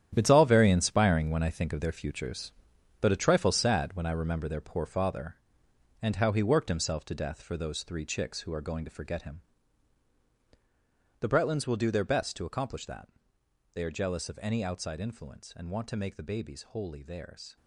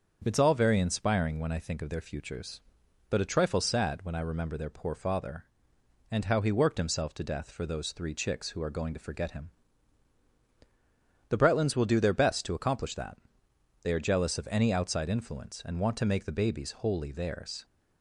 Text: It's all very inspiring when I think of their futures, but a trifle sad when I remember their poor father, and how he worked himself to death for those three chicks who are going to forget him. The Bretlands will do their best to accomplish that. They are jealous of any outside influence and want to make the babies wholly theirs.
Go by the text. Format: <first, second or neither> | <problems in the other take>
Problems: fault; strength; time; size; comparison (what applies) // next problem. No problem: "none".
second | gets quieter; strong; throughout; 11.5 dB // starts louder than the rest; strong; until 1.1 s; 10 dB; also in the second